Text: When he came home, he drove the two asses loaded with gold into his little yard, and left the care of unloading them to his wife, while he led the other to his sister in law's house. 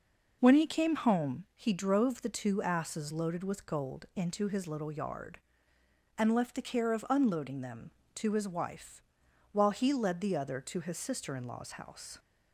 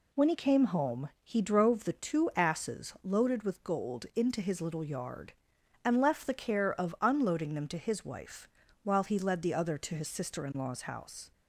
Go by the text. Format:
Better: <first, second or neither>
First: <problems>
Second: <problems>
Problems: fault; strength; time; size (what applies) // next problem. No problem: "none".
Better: neither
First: none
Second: none